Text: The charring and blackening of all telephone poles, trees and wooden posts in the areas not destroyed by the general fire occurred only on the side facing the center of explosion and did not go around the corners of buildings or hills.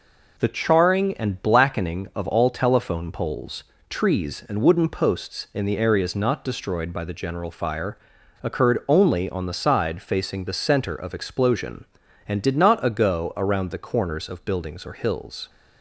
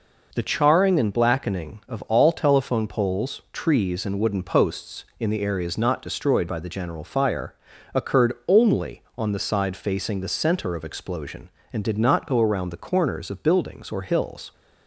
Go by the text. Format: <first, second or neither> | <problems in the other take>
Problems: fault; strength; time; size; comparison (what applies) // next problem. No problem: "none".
second | pauses between "fire" and "occurred"; noticeable; at 7.9 s; 0.46 s long; also in the second // says "ago" for "go"; at 12.8 s